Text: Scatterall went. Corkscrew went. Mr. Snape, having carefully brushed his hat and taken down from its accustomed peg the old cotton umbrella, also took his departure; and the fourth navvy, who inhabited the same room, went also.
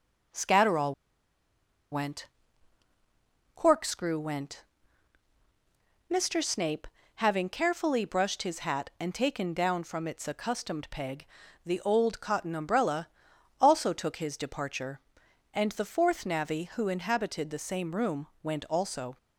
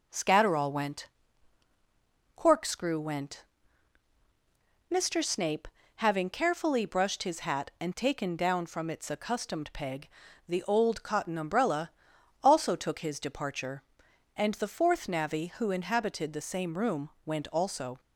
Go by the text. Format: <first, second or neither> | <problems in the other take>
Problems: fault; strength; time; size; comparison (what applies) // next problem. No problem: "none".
second | pauses between "Scatterall" and "went"; at 0.9 s; 0.98 s long // pauses between "peg" and "the"; at 11.2 s; 0.40 s long; also in the second